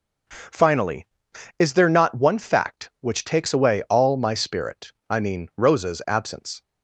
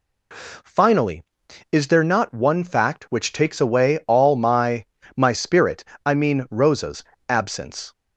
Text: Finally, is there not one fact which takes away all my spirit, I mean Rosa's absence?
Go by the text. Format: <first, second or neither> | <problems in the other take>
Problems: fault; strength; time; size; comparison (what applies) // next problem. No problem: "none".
first | says "my" twice; at 5.1 s // pauses between "Rosa's" and "absence"; slight; at 7.0 s; 0.26 s long